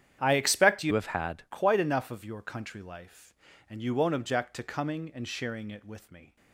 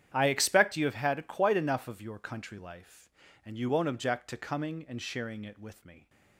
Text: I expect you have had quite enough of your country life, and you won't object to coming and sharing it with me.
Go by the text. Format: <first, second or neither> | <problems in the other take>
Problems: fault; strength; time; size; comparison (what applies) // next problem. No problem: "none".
second | starts louder than the rest; strong; until 1.2 s; 10 dB; strong in the second // changes voice from "have" to "had"; from 0.9 to 1.4 s; 0.5 s long